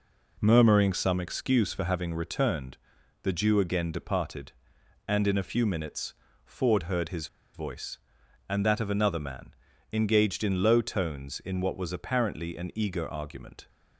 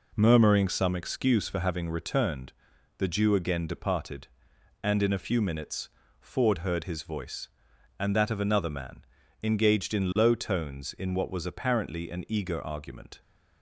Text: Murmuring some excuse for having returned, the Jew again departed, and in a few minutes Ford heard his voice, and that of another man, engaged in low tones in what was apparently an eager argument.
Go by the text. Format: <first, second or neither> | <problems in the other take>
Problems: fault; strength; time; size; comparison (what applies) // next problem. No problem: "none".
second | pauses between "minutes" and "Ford"; slight; at 6.1 s; 0.32 s long; slight in the second // pauses between "his" and "voice"; slight; at 7.2 s; 0.27 s long